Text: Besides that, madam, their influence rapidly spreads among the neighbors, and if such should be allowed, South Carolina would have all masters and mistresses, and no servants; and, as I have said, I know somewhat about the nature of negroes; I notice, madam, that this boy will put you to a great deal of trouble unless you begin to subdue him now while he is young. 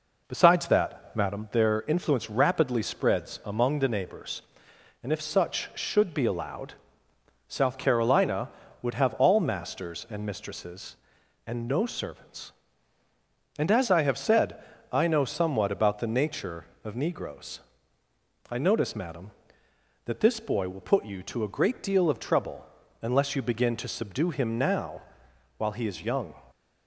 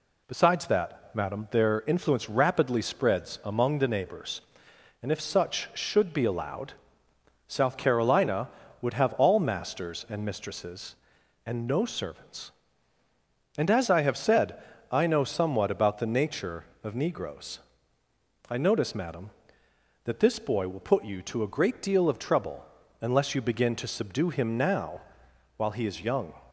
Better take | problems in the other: second | starts louder than the rest; noticeable; until 1.4 s; 4.5 dB // pauses between "trouble" and "unless"; at 22.6 s; 0.38 s long; also in the second // pauses between "now" and "while"; noticeable; at 25.0 s; 0.56 s long; noticeable in the second

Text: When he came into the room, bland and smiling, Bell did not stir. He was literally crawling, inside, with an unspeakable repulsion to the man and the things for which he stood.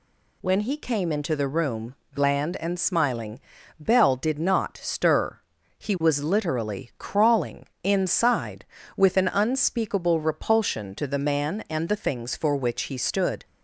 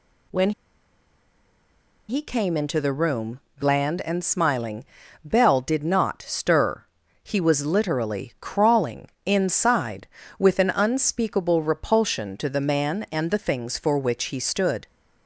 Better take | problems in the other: first | pauses between "When" and "he"; strong; at 0.5 s; 1.5 s long

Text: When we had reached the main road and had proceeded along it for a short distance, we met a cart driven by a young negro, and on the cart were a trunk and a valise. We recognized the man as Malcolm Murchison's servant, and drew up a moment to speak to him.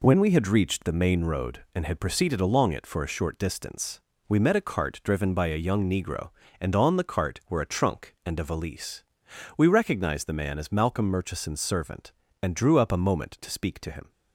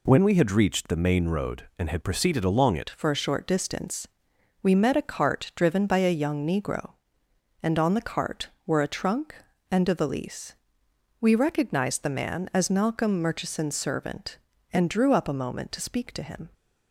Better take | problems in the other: first | changes voice at "for"; from 2.9 s on; 13.5 s long

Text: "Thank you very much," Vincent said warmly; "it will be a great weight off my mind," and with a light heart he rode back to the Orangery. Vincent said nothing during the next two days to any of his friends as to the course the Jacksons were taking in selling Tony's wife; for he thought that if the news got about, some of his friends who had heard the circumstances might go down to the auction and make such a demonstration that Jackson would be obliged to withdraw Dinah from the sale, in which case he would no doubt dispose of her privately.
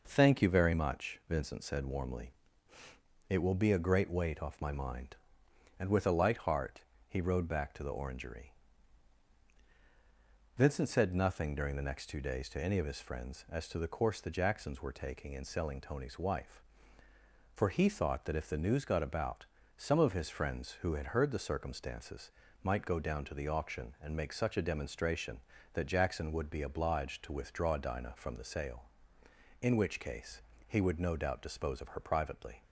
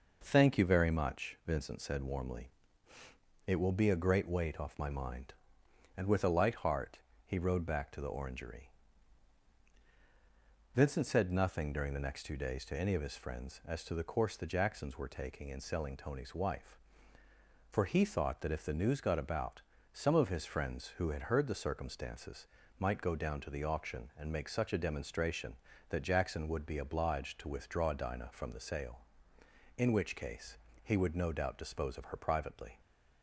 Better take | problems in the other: neither | pauses between "heart" and "he"; slight; the same in both // pauses between "circumstances" and "might"; slight; the same in both // pauses between "case" and "he"; slight; the same in both

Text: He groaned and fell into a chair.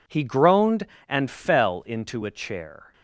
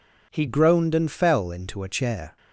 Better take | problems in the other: first | changes voice at "groaned"; from 0.4 s on; 1.9 s long

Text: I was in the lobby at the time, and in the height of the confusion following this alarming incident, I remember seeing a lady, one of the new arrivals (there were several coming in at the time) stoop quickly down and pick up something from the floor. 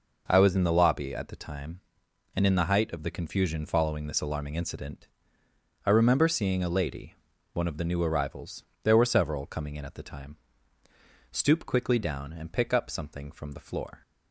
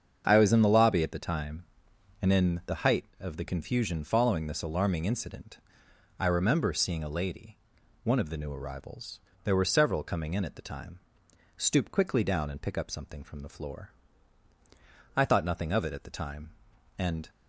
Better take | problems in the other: first | starts louder than the rest; until 1.2 s; 7 dB // goes on to say "I thought nothing of it at the time and"; strong; from 15.1 s on; 2.1 s long

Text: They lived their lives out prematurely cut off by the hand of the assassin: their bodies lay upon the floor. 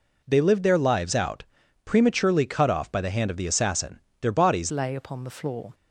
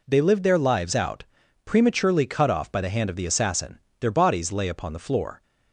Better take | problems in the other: second | pauses between "out" and "prematurely"; at 1.4 s; 0.42 s long; also in the second // changes voice at "lay"; from 4.6 s on; 1.1 s long

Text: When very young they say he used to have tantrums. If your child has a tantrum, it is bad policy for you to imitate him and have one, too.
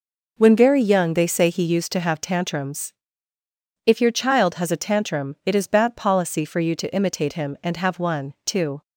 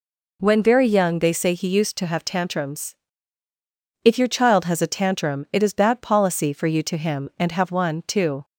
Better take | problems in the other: first | skips "imitate"; at 6.9 s

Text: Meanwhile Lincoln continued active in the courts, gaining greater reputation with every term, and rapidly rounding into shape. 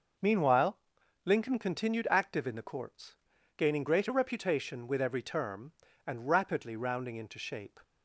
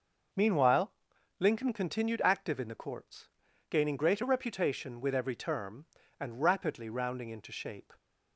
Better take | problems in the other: neither | pauses between "Meanwhile" and "Lincoln"; noticeable; the same in both

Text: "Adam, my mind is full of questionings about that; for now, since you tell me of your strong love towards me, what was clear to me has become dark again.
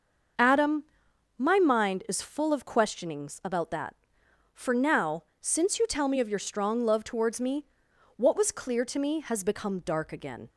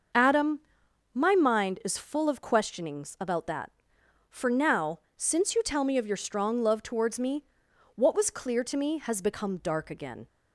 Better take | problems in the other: neither | starts louder than the rest; noticeable; the same in both

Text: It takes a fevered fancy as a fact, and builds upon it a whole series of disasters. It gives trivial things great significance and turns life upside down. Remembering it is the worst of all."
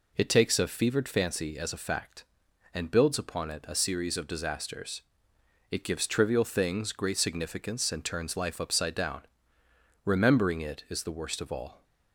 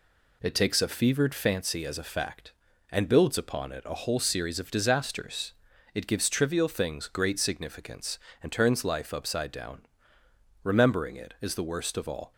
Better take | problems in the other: second | skips "whole"; at 3.7 s

